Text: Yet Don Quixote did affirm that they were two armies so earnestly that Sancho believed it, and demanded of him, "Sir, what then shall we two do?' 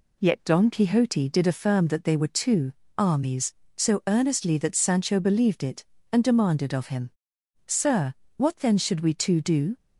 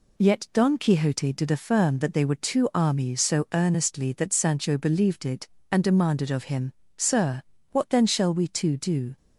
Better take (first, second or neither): second